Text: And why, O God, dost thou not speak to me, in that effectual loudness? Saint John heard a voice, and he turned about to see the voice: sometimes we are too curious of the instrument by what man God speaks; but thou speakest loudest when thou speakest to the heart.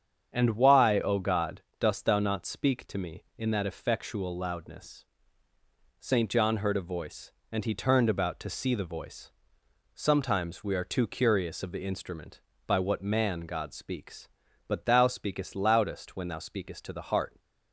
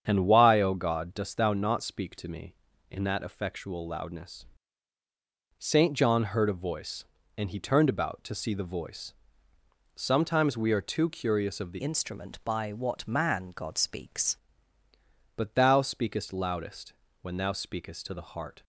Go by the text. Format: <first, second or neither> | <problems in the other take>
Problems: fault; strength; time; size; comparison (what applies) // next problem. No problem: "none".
first | starts louder than the rest; strong; until 1.0 s; 8 dB; strong in the first // changes voice from "instrument" to "speaks"; from 11.8 to 14.3 s; 2.5 s long // pauses between "loudest" and "when"; slight; at 16.9 s; 0.30 s long